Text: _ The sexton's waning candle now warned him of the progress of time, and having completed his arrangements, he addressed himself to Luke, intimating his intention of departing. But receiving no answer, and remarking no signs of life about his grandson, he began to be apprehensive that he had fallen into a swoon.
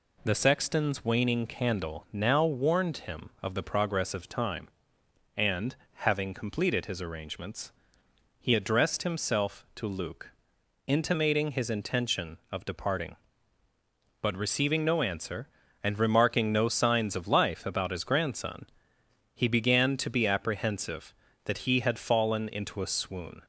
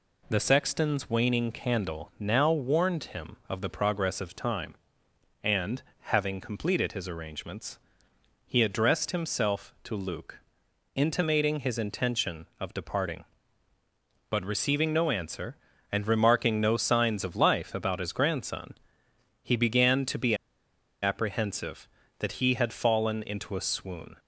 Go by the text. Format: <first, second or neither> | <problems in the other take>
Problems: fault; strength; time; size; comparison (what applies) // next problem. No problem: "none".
first | pauses between "and" and "having"; slight; at 5.8 s; 0.18 s long; slight in the first // pauses between "be" and "apprehensive"; noticeable; at 20.3 s; 0.68 s long